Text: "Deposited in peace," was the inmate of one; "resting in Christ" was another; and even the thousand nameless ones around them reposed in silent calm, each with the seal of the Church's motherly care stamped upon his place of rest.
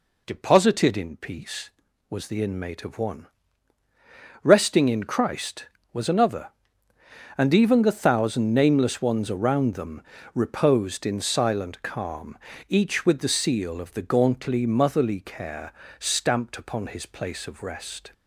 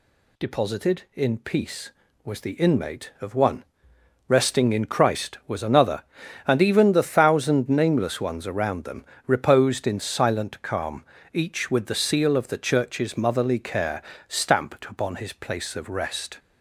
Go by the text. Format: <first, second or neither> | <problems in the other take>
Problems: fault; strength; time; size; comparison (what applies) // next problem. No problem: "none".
second | pauses between "them" and "reposed"; slight; at 10.0 s; 0.32 s long; slight in the second // says "Gauntly" for "Church's"; at 14.0 s // pauses between "care" and "stamped"; slight; at 15.7 s; 0.26 s long; slight in the second